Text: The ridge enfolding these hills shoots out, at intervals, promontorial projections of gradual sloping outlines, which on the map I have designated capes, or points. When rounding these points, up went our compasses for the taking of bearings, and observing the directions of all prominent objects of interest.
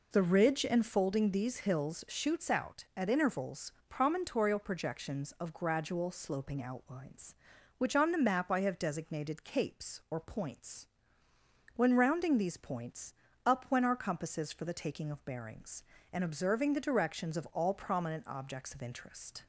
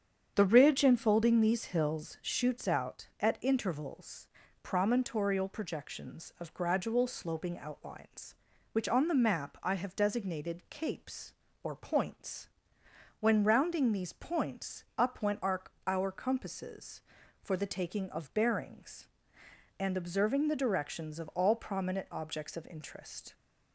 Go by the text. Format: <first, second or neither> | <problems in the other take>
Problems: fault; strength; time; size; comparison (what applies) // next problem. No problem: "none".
first | starts louder than the rest; strong; until 1.3 s; 8 dB // says "our" twice; at 15.8 s